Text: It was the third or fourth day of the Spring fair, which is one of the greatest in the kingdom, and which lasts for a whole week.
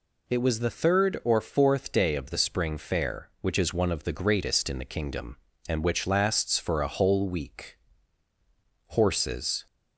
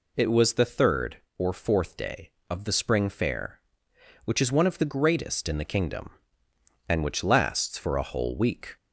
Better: second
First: goes on to say "Horses"; noticeable; from 8.8 s on; 0.78 s long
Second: none

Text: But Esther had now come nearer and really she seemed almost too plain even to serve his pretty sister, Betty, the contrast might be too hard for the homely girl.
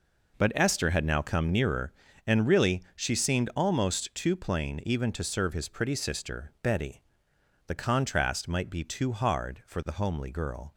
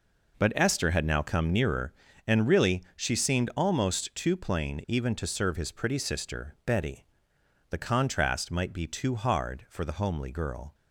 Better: neither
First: none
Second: none

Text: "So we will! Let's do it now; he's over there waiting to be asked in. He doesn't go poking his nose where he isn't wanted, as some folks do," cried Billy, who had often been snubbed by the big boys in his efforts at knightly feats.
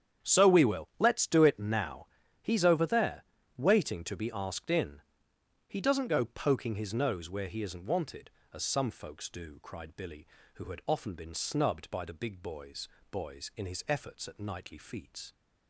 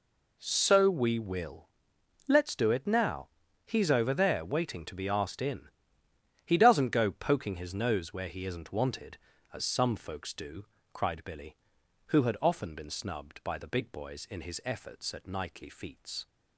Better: second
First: starts louder than the rest; strong; until 1.3 s; 8.5 dB // pauses between "there" and "waiting"; slight; at 3.2 s; 0.34 s long // says "boys" twice; at 13.1 s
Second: none

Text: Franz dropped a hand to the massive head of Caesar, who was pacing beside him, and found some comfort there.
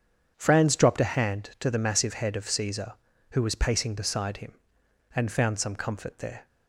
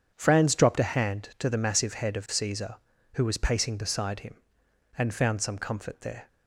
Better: neither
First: none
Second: none

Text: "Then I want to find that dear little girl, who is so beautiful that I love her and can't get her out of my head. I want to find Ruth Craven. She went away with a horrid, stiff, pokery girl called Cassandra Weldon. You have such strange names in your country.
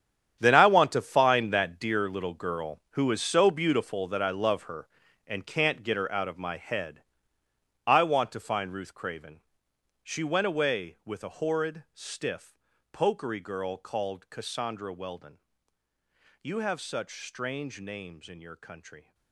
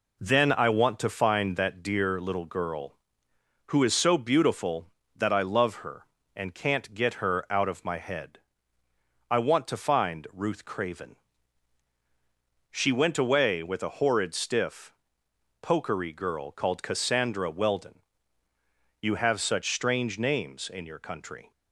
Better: second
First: gets quieter; strong; throughout; 14.5 dB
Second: none

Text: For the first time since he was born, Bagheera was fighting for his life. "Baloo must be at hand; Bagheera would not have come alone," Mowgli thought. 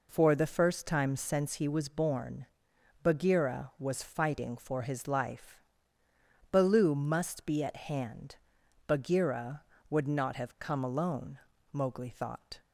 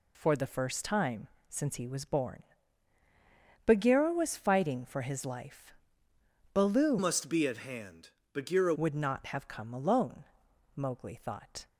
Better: first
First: none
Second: pauses between "time" and "since"; slight; at 1.2 s; 0.22 s long // changes voice from "must" to "Bagheera"; from 6.9 to 8.7 s; 1.8 s long

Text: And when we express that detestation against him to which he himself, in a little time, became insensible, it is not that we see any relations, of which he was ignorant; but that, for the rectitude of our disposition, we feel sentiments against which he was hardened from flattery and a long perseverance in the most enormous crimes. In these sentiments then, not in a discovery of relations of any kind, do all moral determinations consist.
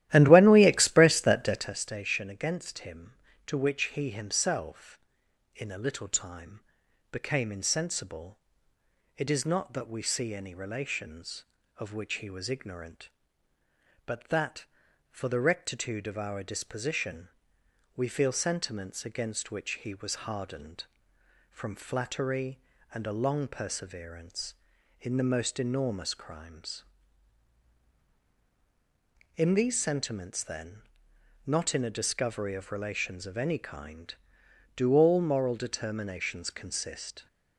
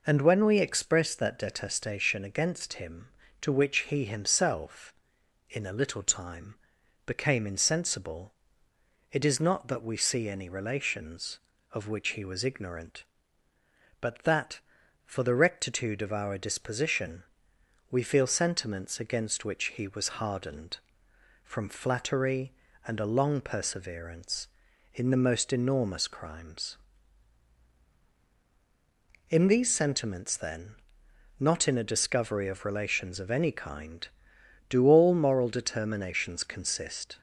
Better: second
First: starts louder than the rest; strong; until 1.7 s; 13.5 dB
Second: none

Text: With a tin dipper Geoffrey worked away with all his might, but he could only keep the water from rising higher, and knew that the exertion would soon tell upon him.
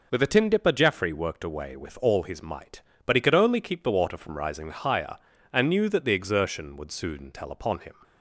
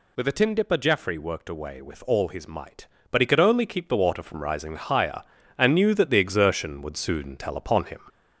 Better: first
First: none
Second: gets louder; slight; throughout; 3.5 dB

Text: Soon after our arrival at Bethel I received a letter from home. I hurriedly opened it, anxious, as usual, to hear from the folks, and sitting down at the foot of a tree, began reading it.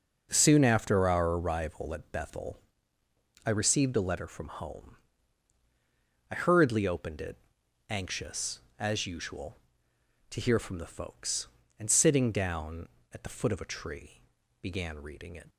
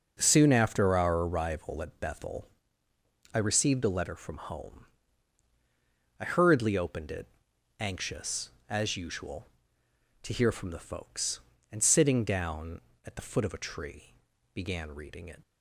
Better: neither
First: pauses between "Bethel" and "I"; noticeable; at 2.5 s; 0.84 s long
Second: pauses between "Bethel" and "I"; noticeable; at 2.4 s; 0.84 s long

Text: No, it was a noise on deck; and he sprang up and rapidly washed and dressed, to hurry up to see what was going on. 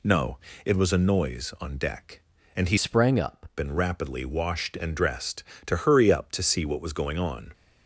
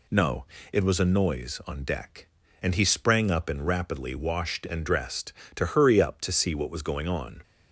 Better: second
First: changes voice from "sprang" to "up"; from 2.7 to 3.4 s; 0.7 s long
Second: none

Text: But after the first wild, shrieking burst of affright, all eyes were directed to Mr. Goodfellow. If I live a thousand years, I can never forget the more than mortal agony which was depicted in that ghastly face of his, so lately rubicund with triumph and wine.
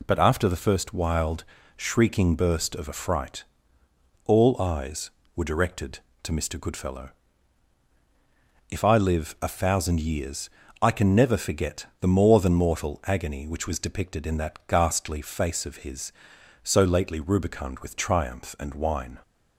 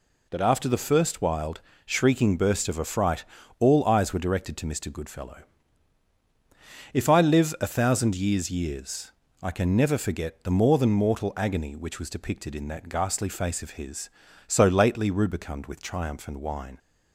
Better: first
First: none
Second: says "years" twice; at 8.5 s

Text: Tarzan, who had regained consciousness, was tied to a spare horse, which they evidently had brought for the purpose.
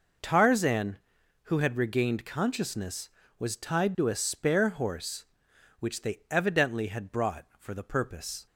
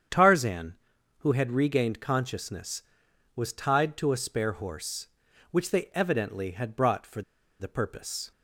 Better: first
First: none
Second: starts louder than the rest; strong; until 1.5 s; 8 dB // pauses between "for" and "the"; at 7.2 s; 0.38 s long

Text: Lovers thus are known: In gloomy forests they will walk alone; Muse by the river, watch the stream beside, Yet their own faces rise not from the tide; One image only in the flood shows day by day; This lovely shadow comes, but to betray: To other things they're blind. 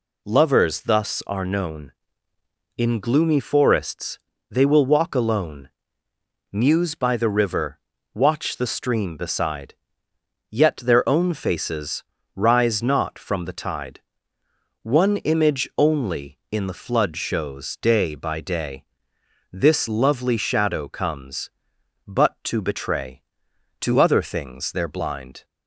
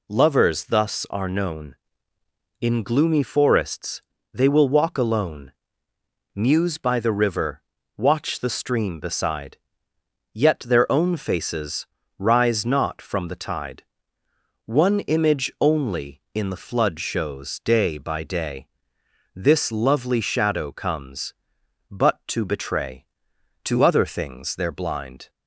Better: neither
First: pauses between "forests" and "they"; slight; at 4.1 s; 0.32 s long // pauses between "faces" and "rise"; slight; at 12.0 s; 0.32 s long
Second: pauses between "forests" and "they"; slight; at 4.0 s; 0.32 s long // pauses between "faces" and "rise"; slight; at 11.8 s; 0.32 s long

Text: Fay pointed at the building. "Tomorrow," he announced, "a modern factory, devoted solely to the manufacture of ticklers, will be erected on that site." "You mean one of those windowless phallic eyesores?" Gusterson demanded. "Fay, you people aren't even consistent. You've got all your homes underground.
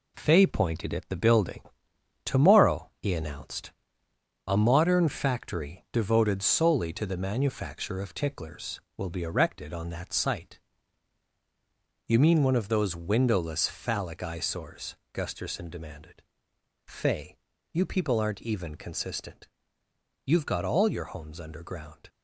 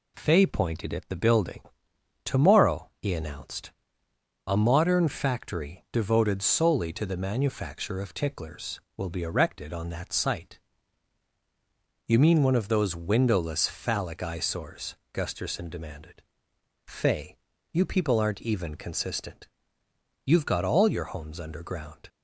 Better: second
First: gets quieter; throughout; 6 dB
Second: none

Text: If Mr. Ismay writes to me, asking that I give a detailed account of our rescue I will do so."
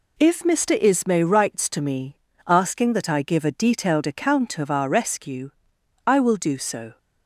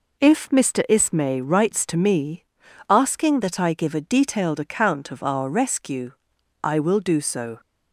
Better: neither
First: pauses between "rescue" and "I"; noticeable; at 5.5 s; 0.56 s long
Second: pauses between "rescue" and "I"; noticeable; at 6.0 s; 0.54 s long

